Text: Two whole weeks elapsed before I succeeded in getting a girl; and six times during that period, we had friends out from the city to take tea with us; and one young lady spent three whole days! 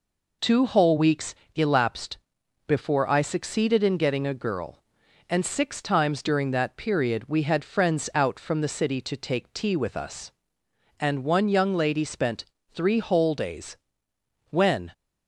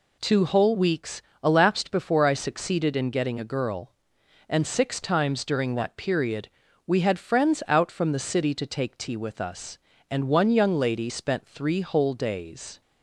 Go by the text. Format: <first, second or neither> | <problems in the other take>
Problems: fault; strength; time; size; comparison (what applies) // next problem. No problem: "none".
second | pauses between "weeks" and "elapsed"; slight; at 1.3 s; 0.22 s long; slight in the second // pauses between "elapsed" and "before"; noticeable; at 2.1 s; 0.50 s long // pauses between "spent" and "three"; slight; at 12.4 s; 0.32 s long // goes on to say "When"; slight; from 14.4 s on; 0.42 s long